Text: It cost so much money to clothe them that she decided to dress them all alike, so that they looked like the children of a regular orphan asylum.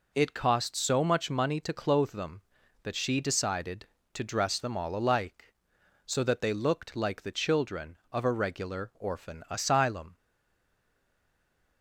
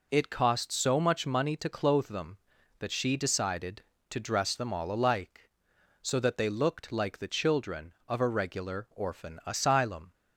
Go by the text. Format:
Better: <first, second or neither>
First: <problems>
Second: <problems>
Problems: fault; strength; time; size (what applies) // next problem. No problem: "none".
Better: second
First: stays silent after the last word; noticeable; from 10.1 s on; 1.7 s long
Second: none